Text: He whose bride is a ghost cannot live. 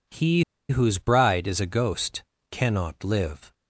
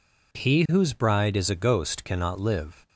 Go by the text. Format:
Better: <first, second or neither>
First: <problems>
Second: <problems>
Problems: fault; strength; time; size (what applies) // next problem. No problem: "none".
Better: second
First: pauses between "He" and "whose"; slight; at 0.4 s; 0.25 s long // pauses between "ghost" and "cannot"; slight; at 2.2 s; 0.28 s long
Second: none